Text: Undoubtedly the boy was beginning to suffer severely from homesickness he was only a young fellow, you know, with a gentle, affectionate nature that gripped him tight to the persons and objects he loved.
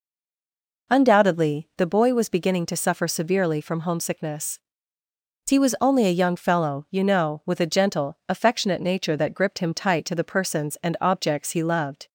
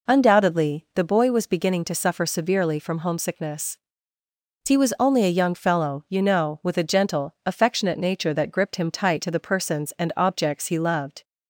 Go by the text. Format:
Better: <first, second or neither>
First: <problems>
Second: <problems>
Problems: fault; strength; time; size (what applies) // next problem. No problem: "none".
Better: second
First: stays silent before the first word; slight; until 0.8 s; 0.8 s long // pauses between "homesickness" and "he"; noticeable; at 4.5 s; 0.88 s long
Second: pauses between "homesickness" and "he"; noticeable; at 3.7 s; 0.88 s long